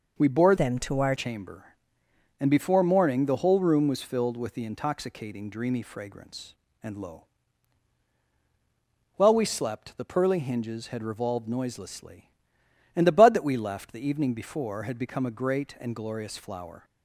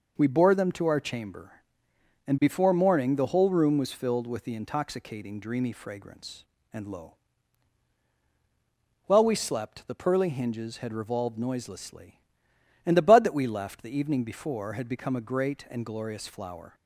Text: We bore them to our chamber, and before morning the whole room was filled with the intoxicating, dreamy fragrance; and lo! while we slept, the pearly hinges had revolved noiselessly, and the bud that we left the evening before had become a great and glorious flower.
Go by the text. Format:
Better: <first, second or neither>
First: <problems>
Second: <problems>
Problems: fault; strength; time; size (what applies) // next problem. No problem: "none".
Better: second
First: changes voice from "them" to "our"; from 0.5 to 1.1 s; 0.6 s long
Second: none